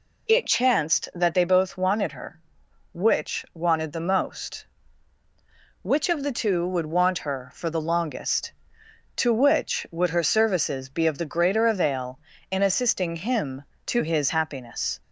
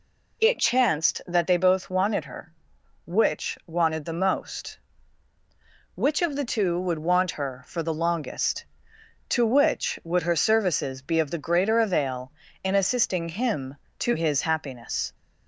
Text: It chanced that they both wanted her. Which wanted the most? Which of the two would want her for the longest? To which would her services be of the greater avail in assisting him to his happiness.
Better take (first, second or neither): neither